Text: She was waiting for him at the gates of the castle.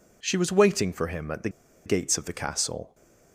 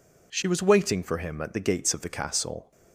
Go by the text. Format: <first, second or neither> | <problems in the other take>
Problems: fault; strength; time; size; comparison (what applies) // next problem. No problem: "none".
second | pauses between "the" and "gates"; at 1.4 s; 0.37 s long